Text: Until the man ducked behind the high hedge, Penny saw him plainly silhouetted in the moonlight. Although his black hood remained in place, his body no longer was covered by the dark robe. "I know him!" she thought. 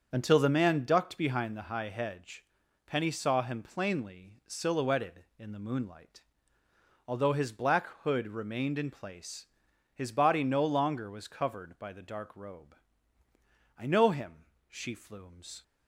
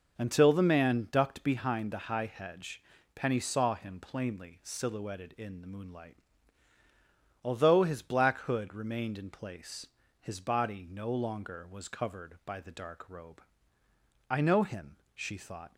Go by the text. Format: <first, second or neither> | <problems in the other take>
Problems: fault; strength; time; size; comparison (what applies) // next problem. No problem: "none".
second | starts louder than the rest; until 1.1 s; 6.5 dB // pauses between "black" and "hood"; slight; at 7.8 s; 0.16 s long // says "flumes" for "thought"; at 14.9 s